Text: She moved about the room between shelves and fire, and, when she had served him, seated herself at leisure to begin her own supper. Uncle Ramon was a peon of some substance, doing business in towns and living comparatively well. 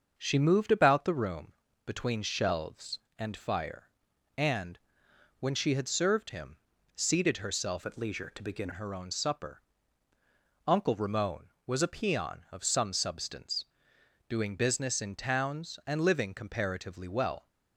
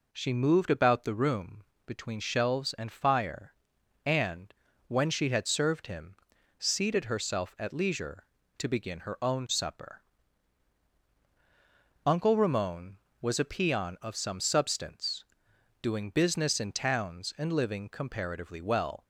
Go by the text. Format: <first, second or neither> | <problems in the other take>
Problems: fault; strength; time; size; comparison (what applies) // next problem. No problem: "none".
second | starts louder than the rest; until 1.1 s; 6.5 dB // pauses between "room" and "between"; slight; at 1.5 s; 0.32 s long; slight in the second // changes voice from "at" to "begin"; from 7.8 to 8.6 s; 0.8 s long